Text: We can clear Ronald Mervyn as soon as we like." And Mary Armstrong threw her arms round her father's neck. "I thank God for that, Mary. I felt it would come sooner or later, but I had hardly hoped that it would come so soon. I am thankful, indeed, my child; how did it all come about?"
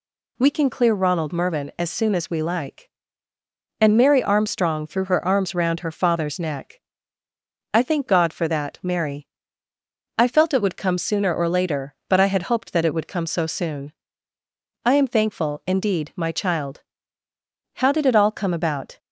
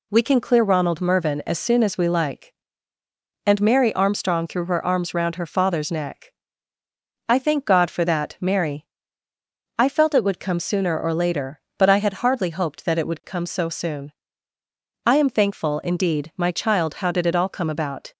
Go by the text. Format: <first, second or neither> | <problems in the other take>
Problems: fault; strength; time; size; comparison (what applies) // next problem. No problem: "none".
second | skips "hardly"; at 12.4 s